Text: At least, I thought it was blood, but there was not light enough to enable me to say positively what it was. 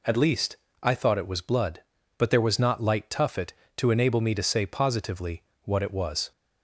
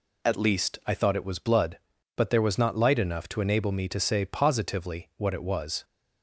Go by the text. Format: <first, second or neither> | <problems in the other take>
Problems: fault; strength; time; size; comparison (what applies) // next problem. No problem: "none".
second | says "tuffet" for "enough"; at 3.0 s // pauses between "positively" and "what"; slight; at 5.4 s; 0.22 s long